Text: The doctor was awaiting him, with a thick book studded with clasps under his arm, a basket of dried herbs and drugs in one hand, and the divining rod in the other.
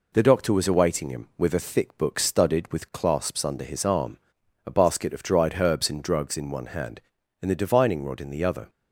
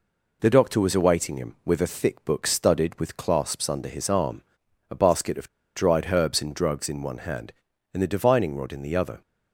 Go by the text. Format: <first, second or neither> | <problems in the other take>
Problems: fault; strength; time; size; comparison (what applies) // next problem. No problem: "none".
first | pauses between "of" and "dried"; slight; at 5.4 s; 0.28 s long